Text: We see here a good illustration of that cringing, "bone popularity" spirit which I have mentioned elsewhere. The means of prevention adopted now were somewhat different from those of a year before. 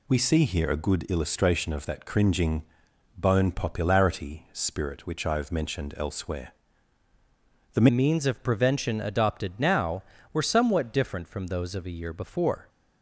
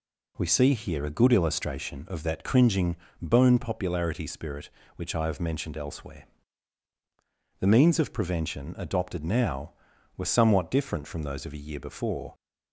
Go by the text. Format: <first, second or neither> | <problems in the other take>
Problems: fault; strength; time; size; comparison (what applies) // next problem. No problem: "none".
second | changes voice at "means"; from 7.8 s on; 4.8 s long